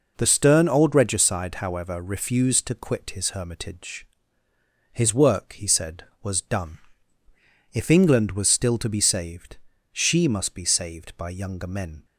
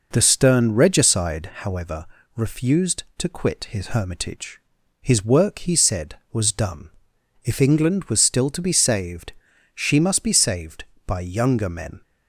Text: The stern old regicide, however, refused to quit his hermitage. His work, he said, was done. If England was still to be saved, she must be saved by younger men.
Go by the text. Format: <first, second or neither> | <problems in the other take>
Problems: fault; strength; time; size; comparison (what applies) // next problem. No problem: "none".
first | skips "old"; at 0.7 s